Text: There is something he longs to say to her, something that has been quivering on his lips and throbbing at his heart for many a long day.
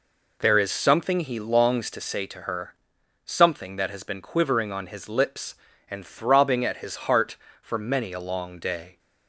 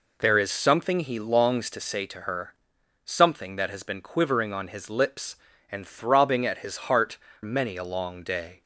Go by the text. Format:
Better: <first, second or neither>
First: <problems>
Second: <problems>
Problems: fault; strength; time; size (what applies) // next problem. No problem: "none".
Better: first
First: none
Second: skips "for"; at 7.3 s